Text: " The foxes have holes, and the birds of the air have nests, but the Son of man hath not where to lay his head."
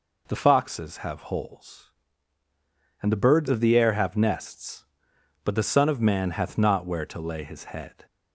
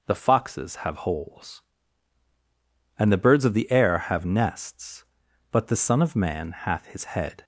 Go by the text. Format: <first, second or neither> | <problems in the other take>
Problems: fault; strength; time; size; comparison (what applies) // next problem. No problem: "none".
first | skips "not where to lay"; at 6.8 s